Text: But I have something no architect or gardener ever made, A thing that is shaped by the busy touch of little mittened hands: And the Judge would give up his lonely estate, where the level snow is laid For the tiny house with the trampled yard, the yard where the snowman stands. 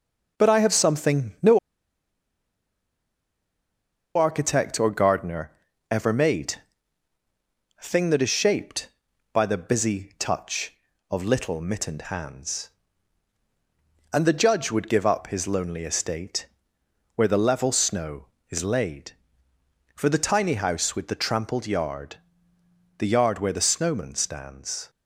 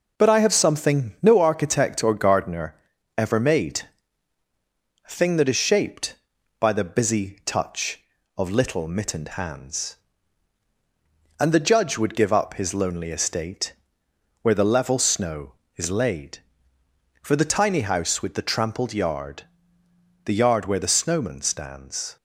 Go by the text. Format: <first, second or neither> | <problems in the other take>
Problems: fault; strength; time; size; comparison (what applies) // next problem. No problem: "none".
second | pauses between "no" and "architect"; strong; at 1.5 s; 2.5 s long // pauses between "gardener" and "ever"; at 5.5 s; 0.40 s long; also in the second